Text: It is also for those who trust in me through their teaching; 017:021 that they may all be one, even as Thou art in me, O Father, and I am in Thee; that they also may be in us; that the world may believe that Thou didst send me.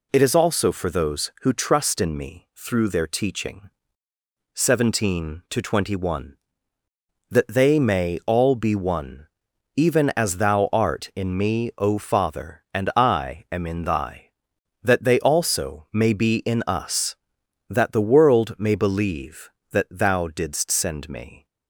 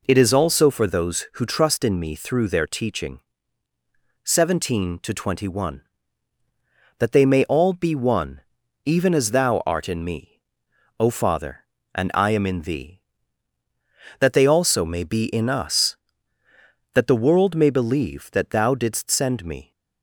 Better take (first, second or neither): second